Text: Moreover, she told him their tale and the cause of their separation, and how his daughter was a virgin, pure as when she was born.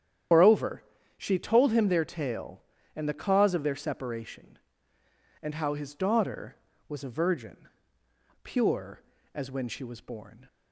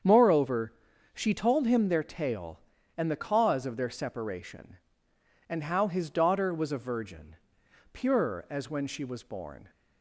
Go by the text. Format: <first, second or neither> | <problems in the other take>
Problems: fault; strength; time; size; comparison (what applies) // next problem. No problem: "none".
second | loses the start of "Moreover"; at 0.3 s; 140 ms // starts louder than the rest; strong; until 1.6 s; 9.5 dB; strong in the second